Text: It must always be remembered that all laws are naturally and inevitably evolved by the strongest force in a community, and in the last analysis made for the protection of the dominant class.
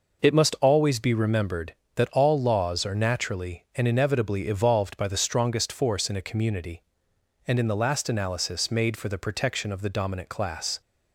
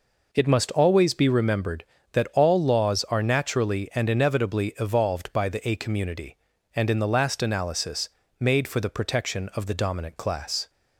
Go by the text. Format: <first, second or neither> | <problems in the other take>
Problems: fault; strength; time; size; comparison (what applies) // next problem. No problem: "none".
first | skips "strongest force in"; at 5.6 s // pauses between "analysis" and "made"; slight; at 8.0 s; 0.30 s long